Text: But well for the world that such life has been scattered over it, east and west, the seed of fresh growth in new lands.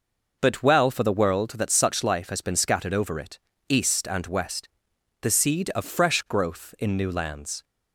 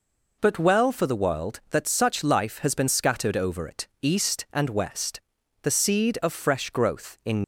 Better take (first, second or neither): first